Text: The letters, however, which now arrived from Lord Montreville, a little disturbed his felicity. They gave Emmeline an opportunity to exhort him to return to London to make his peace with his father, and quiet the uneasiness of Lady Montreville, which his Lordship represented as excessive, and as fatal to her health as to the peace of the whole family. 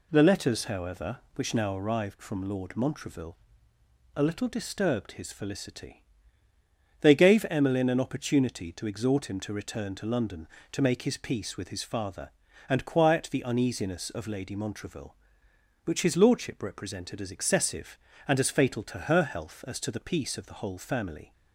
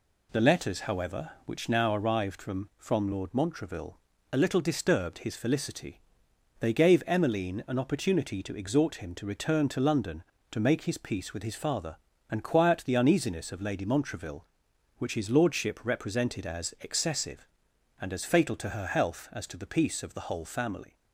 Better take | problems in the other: first | says "from" twice; at 2.7 s

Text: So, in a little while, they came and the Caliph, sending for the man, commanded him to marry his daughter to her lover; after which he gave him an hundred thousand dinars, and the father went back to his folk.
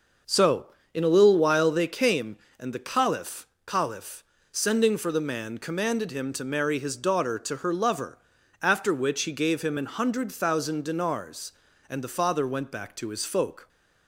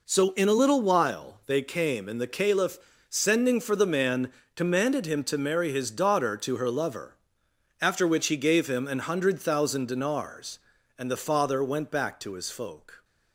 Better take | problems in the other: second | starts louder than the rest; until 1.5 s; 6.5 dB // says "Caliph" twice; at 3.6 s

